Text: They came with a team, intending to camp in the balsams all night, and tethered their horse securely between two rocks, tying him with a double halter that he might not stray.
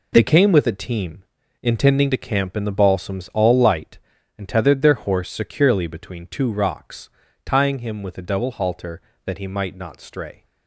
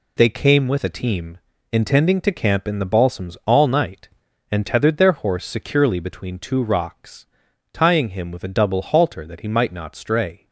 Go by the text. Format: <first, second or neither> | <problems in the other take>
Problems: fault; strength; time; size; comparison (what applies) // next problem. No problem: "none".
second | says "light" for "night"; at 3.5 s